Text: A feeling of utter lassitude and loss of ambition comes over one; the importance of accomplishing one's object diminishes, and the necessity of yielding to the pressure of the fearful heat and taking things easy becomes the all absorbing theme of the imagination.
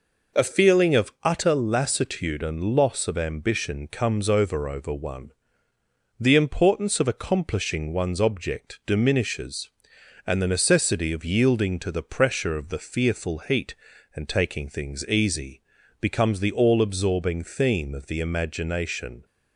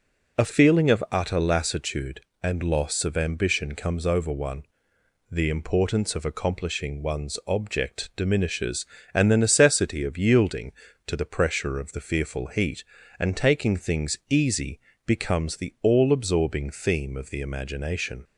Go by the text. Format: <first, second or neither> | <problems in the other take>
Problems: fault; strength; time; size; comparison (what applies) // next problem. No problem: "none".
second | says "over" twice; at 4.6 s // pauses between "easy" and "becomes"; at 15.6 s; 0.40 s long; slight in the second